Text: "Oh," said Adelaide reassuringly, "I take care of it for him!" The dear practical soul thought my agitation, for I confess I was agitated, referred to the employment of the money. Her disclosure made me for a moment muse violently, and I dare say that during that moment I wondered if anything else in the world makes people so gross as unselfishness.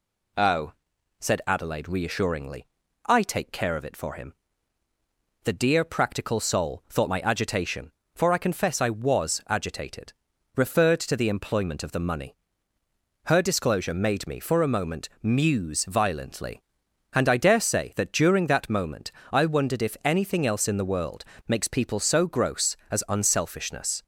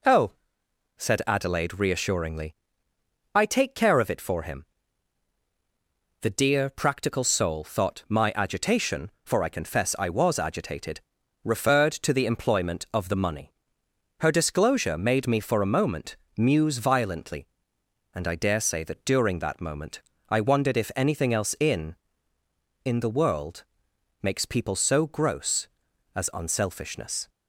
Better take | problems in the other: first | pauses between "moment" and "muse"; slight; at 16.1 s; 0.20 s long // pauses between "moment" and "I"; slight; at 20.0 s; 0.28 s long; slight in the first // says "in" twice; at 22.8 s // pauses between "world" and "makes"; noticeable; at 23.6 s; 0.58 s long; slight in the first

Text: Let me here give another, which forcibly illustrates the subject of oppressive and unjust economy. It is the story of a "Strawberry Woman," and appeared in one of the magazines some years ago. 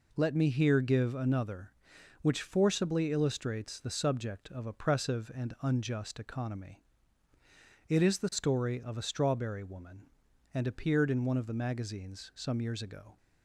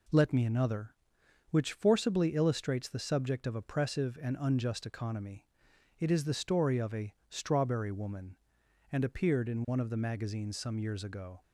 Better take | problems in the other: first | skips "here give"; at 0.4 s // pauses between "a" and "Strawberry"; slight; at 7.1 s; 0.16 s long

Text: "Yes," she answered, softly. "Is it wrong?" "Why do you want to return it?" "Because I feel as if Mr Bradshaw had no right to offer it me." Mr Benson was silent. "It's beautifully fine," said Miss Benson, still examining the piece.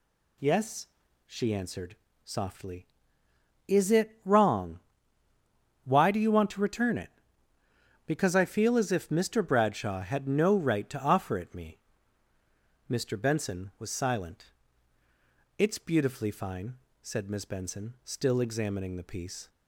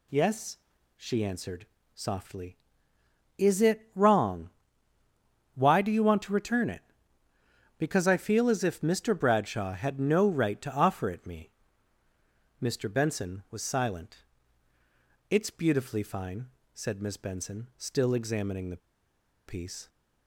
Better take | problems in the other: first | pauses between "the" and "piece"; noticeable; at 18.7 s; 0.67 s long

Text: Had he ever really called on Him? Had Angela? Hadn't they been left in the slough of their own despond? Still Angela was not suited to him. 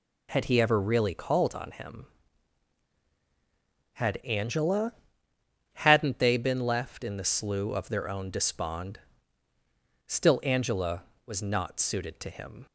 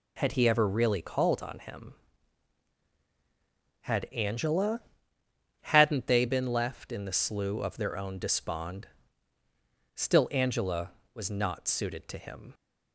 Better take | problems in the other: neither | none

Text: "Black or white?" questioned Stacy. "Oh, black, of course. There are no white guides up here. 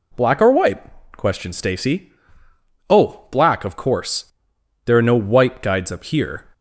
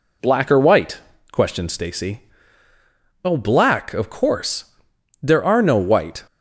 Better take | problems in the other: first | stops before "guides up here"; at 6.2 s

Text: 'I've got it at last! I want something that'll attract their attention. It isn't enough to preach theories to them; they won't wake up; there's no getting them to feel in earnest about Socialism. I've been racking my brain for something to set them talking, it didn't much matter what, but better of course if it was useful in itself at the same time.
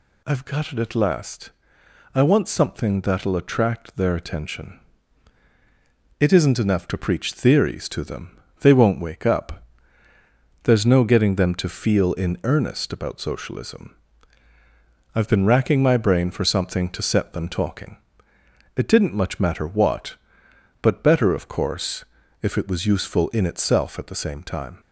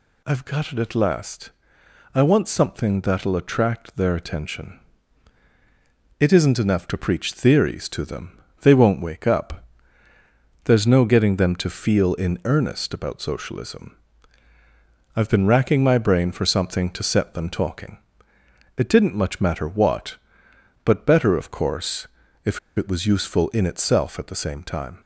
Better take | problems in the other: first | pauses between "course" and "if"; at 22.0 s; 0.38 s long; also in the first // pauses between "if" and "it"; slight; at 22.5 s; 0.19 s long

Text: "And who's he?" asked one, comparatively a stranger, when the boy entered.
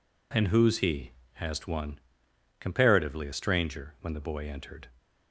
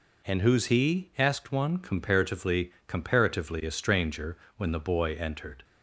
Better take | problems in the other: first | says "comparatively" twice; at 2.8 s

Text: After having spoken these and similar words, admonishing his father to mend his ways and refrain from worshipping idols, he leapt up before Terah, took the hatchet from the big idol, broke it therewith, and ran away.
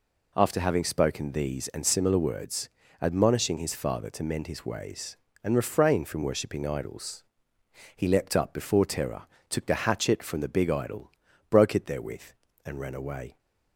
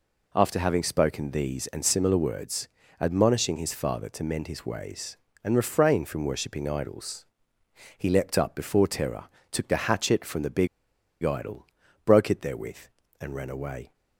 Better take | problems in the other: first | pauses between "big" and "idol"; noticeable; at 10.6 s; 0.55 s long

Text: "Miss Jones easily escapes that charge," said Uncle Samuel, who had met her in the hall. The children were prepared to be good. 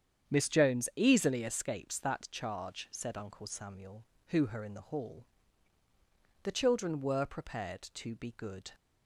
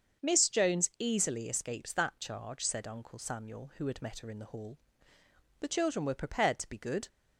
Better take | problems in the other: second | starts louder than the rest; strong; until 1.3 s; 8 dB; also in the second // skips "had met"; at 4.4 s

